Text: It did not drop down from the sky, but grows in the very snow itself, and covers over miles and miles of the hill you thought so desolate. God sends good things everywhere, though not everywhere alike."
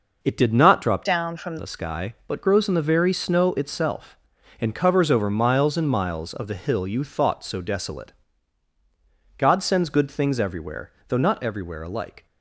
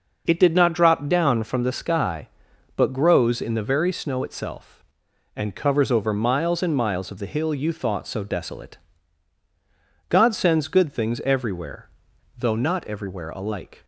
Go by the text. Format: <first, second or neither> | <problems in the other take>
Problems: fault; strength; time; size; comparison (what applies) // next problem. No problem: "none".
second | changes voice from "down" to "from"; from 1.0 to 1.5 s; 0.5 s long